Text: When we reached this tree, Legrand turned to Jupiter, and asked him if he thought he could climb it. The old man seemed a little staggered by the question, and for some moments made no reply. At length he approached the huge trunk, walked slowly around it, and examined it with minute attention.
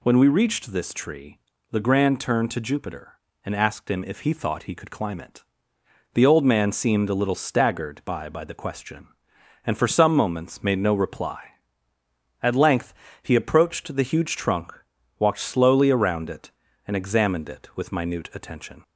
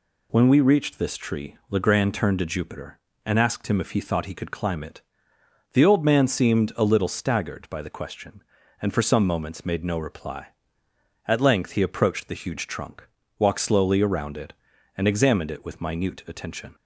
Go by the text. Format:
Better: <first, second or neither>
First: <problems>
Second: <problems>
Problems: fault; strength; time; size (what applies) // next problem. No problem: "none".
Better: second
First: says "by" twice; at 8.2 s // pauses between "length" and "he"; slight; at 12.9 s; 0.30 s long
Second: none